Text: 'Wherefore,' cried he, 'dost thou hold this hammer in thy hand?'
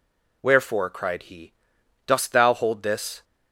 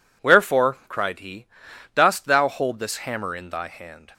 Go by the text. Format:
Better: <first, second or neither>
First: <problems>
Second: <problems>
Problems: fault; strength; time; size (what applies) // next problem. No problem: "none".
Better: second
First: stops before "hammer in thy hand"; at 3.2 s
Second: none